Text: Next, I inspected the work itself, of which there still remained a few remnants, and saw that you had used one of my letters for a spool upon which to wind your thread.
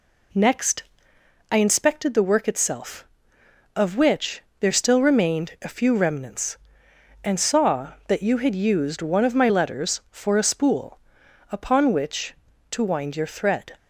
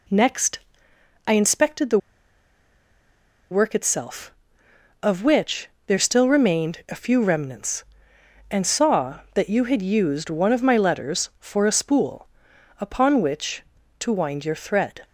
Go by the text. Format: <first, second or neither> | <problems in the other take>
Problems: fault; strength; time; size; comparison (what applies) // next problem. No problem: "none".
first | pauses between "the" and "work"; strong; at 1.9 s; 1.5 s long // pauses between "which" and "there"; slight; at 5.6 s; 0.20 s long; slight in the first // pauses between "spool" and "upon"; noticeable; at 12.2 s; 0.50 s long; noticeable in the first